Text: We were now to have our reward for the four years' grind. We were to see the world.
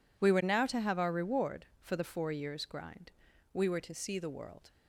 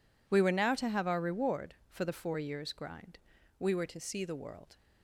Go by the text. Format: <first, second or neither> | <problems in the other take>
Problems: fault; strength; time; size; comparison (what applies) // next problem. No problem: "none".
neither | none